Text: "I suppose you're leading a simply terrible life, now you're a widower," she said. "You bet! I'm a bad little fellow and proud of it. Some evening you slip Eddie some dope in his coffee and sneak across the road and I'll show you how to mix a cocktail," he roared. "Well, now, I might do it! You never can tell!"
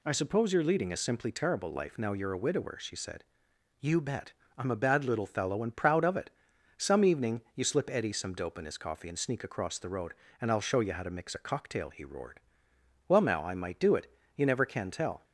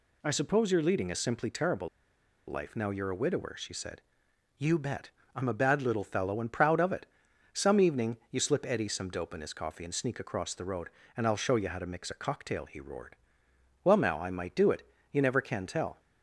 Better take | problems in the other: first | pauses between "terrible" and "life"; noticeable; at 1.8 s; 0.60 s long

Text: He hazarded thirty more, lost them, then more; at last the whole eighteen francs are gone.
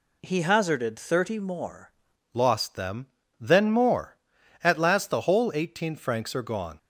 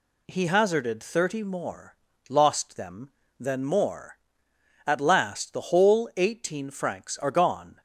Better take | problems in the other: second | changes voice at "lost"; from 2.3 s on; 4.4 s long

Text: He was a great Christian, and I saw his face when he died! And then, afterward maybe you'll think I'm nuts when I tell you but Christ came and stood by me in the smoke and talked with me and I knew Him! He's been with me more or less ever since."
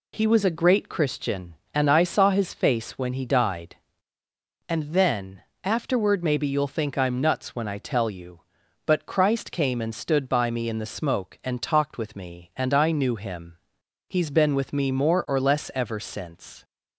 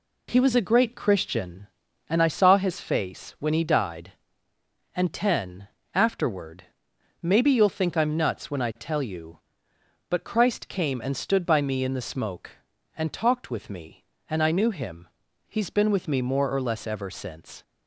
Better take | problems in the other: first | says "ten" for "then"; at 5.1 s // pauses between "afterward" and "maybe"; noticeable; at 6.6 s; 0.54 s long

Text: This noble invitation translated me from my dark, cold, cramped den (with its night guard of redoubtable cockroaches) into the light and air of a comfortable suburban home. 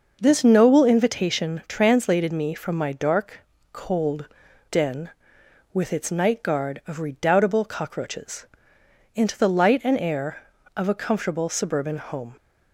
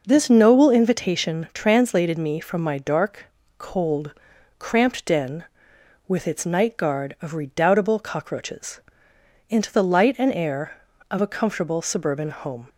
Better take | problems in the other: second | skips "cramped"; at 4.4 s

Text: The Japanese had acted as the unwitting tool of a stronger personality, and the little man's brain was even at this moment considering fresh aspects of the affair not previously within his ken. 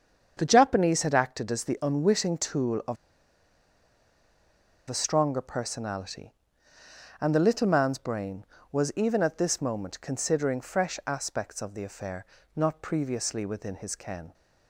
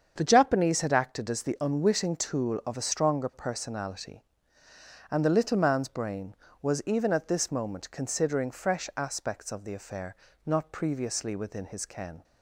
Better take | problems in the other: second | starts louder than the rest; strong; until 1.3 s; 7.5 dB; strong in the second // pauses between "of" and "a"; strong; at 2.9 s; 1.9 s long // pauses between "affair" and "not"; slight; at 12.2 s; 0.30 s long; slight in the second

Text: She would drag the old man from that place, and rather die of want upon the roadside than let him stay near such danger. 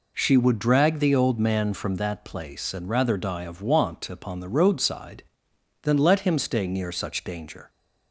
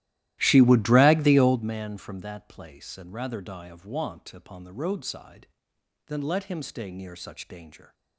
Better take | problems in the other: first | starts louder than the rest; strong; until 1.8 s; 15 dB

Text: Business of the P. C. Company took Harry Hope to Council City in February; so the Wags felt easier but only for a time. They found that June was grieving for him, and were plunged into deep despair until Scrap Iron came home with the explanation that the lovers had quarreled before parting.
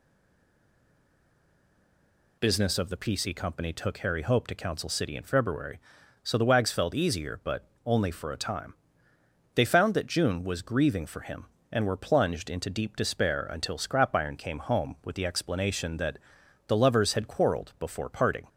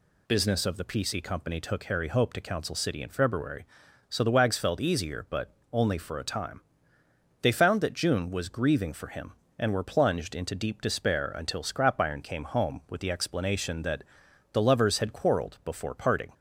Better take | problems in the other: second | stays silent before the first word; until 2.3 s; 2.3 s long // pauses between "but" and "only"; slight; at 7.6 s; 0.17 s long; slight in the second // pauses between "that" and "the"; noticeable; at 16.1 s; 0.48 s long; noticeable in the second

